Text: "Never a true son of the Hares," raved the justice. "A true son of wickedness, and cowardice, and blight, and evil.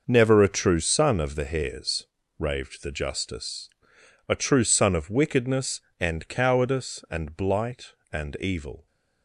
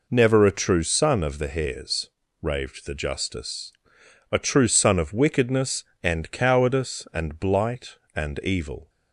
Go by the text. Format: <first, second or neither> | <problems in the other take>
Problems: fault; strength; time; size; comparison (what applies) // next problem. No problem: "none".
second | gets quieter; strong; throughout; 10 dB